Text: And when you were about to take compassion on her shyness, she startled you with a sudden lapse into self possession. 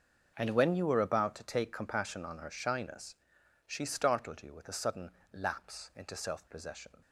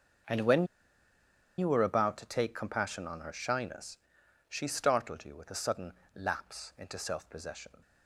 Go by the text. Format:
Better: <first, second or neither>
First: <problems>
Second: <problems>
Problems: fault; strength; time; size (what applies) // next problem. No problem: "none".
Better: first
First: starts louder than the rest; until 1.3 s; 6 dB // pauses between "sudden" and "lapse"; slight; at 5.1 s; 0.20 s long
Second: starts louder than the rest; until 2.2 s; 6 dB // pauses between "when" and "you"; noticeable; at 0.6 s; 0.93 s long // pauses between "sudden" and "lapse"; slight; at 5.9 s; 0.20 s long